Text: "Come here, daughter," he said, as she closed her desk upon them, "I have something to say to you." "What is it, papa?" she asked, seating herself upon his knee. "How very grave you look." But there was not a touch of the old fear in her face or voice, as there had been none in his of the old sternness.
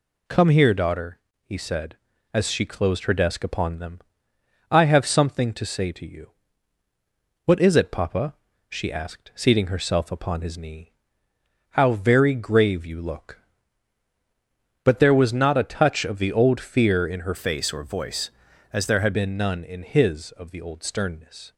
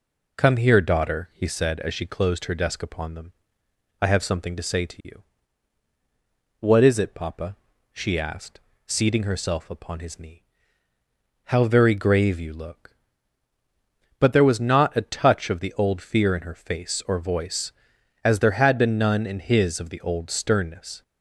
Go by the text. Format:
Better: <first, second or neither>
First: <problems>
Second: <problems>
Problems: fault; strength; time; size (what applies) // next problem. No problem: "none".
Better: second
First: changes voice from "face" to "had"; from 17.3 to 19.1 s; 1.8 s long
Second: none